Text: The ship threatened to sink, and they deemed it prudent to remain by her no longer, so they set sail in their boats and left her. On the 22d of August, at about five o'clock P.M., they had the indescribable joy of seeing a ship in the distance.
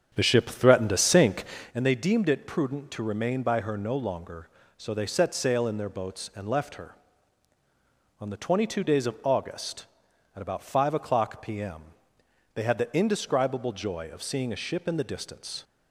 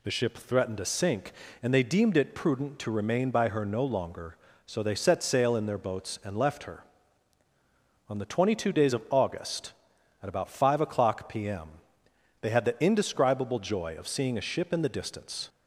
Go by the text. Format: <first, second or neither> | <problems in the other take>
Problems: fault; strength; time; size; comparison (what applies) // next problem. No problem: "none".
second | starts louder than the rest; strong; until 1.8 s; 8 dB